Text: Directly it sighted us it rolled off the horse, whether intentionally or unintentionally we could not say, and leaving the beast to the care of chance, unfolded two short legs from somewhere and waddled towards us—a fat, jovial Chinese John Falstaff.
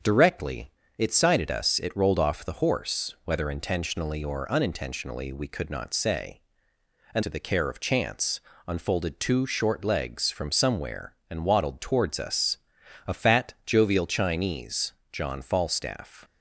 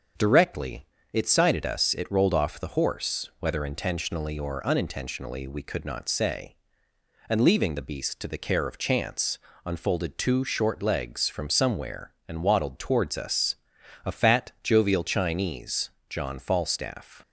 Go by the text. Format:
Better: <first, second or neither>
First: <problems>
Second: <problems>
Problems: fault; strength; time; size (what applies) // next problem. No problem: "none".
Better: second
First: starts louder than the rest; strong; until 1.3 s; 7.5 dB // pauses between "Directly" and "it"; slight; at 0.6 s; 0.28 s long // skips "leaving the beast"; at 7.2 s // pauses between "Chinese" and "John"; slight; at 14.9 s; 0.20 s long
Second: starts louder than the rest; until 1.4 s; 7 dB // pauses between "Directly" and "it"; slight; at 0.8 s; 0.28 s long // pauses between "Chinese" and "John"; slight; at 15.8 s; 0.20 s long